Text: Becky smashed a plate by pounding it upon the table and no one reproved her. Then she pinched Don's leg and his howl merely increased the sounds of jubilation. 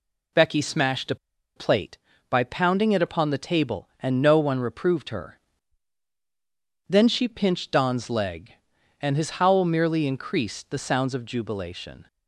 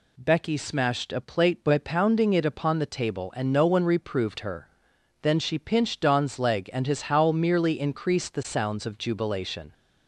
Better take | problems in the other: second | pauses between "a" and "plate"; at 1.1 s; 0.41 s long

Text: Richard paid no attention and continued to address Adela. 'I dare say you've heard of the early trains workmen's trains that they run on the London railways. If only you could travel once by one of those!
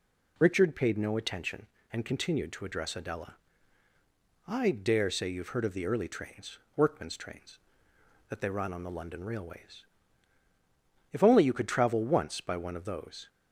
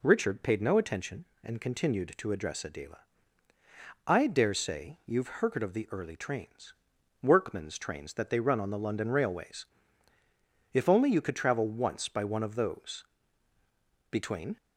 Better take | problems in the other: first | pauses between "trains" and "workmen's"; noticeable; at 6.7 s; 0.50 s long; slight in the first // goes on to say "Between"; slight; from 14.1 s on; 0.46 s long

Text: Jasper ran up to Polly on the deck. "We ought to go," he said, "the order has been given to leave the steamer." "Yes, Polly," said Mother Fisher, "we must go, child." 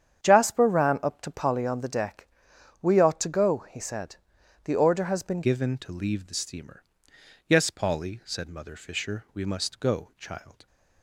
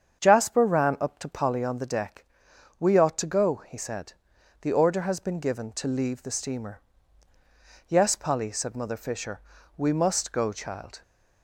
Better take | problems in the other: second | starts louder than the rest; strong; until 1.2 s; 8.5 dB; strong in the second // changes voice at "given"; from 5.4 s on; 5.2 s long

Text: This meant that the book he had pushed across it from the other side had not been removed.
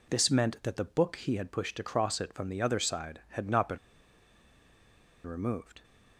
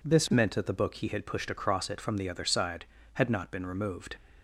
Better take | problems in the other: second | pauses between "been" and "removed"; strong; at 3.7 s; 1.4 s long

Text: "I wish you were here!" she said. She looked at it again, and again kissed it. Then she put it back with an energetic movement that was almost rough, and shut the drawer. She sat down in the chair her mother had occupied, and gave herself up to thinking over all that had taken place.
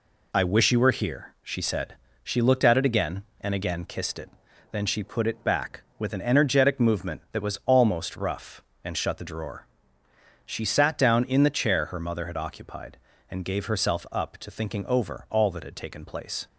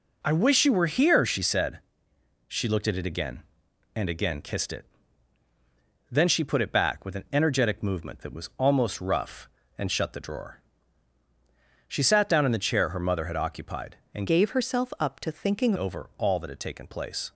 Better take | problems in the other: first | changes voice from "gave" to "thinking"; from 14.2 to 15.7 s; 1.5 s long

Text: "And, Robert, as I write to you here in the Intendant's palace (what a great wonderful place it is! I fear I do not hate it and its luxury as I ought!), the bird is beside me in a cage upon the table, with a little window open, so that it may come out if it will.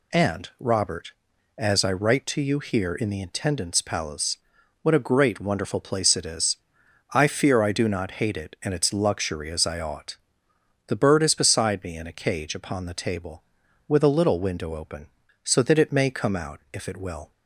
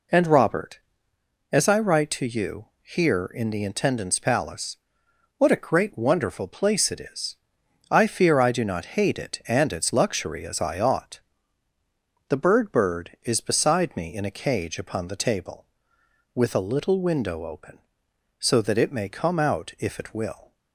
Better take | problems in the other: first | pauses between "you" and "here"; slight; at 2.6 s; 0.16 s long // says "bird" twice; at 12.7 s

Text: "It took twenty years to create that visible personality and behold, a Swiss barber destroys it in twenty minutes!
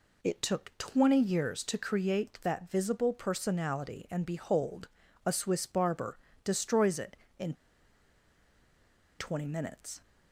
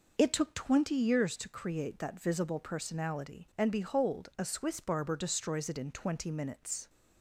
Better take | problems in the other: second | pauses between "barber" and "destroys"; slight; at 6.1 s; 0.26 s long // pauses between "in" and "twenty"; strong; at 7.5 s; 1.6 s long

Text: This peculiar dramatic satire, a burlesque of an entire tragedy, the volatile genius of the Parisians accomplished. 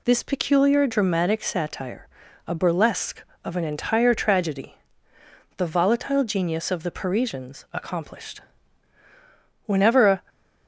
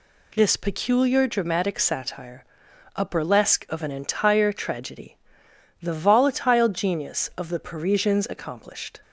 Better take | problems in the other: second | goes on to say "Whenever a"; from 9.6 s on; 0.58 s long

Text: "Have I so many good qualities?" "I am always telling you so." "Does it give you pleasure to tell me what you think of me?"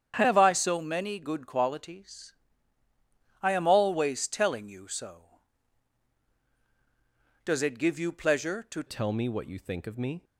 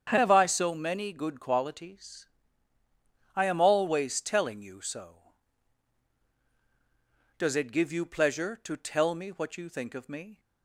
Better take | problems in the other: second | starts louder than the rest; strong; until 1.1 s; 8.5 dB; strong in the second // changes voice at "tell"; from 8.8 s on; 1.4 s long

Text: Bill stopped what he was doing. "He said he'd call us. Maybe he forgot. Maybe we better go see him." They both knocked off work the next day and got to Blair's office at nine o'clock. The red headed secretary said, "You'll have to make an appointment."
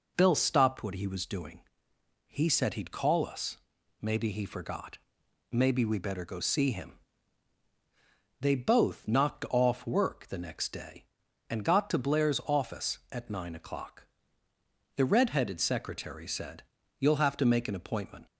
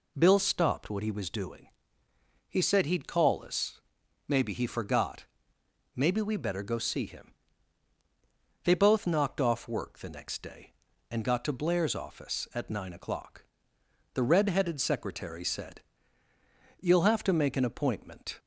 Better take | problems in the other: neither | none

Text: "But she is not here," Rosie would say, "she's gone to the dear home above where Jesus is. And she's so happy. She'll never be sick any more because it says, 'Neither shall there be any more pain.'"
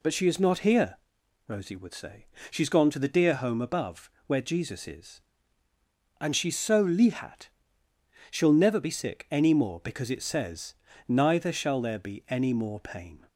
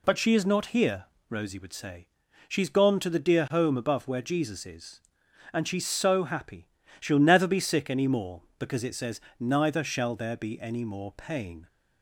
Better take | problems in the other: second | pauses between "above" and "where"; slight; at 4.0 s; 0.18 s long // says "lihat" for "happy"; at 6.8 s

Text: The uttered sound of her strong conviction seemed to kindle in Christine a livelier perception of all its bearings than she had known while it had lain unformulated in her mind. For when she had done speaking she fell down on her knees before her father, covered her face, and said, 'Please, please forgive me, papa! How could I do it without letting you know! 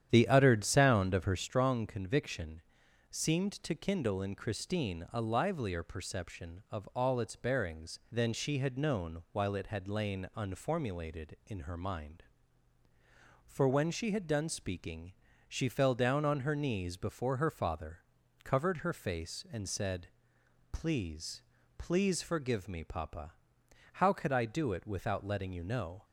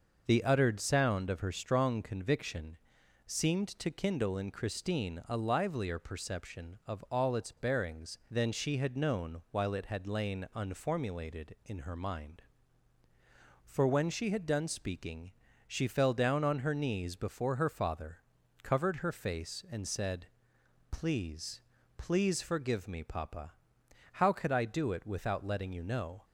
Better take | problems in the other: second | starts louder than the rest; strong; until 1.5 s; 9.5 dB // pauses between "conviction" and "seemed"; noticeable; at 2.6 s; 0.48 s long; noticeable in the second // pauses between "speaking" and "she"; slight; at 15.1 s; 0.34 s long; slight in the second

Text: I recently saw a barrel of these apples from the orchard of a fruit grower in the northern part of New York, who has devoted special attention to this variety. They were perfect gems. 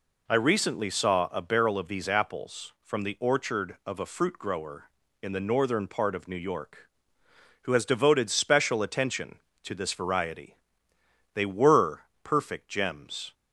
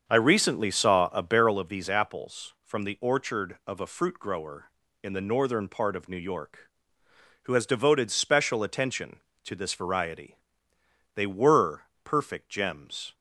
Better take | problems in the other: first | starts louder than the rest; until 1.6 s; 7 dB // pauses between "were" and "perfect"; slight; at 11.8 s; 0.18 s long; slight in the first

